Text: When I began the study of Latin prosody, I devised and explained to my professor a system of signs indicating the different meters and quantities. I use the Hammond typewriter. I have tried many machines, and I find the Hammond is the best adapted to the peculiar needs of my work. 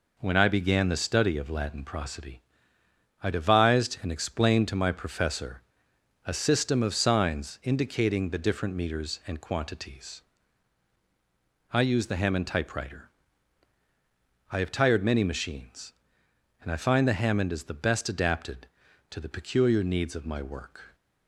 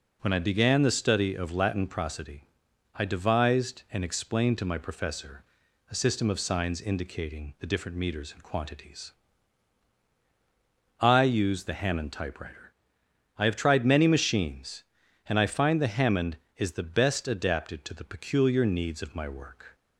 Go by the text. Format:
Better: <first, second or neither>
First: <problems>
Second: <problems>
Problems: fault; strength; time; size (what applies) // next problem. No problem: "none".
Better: second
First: pauses between "professor" and "a"; noticeable; at 5.6 s; 0.64 s long // says "tired" for "tried"; at 14.7 s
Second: pauses between "professor" and "a"; noticeable; at 5.4 s; 0.46 s long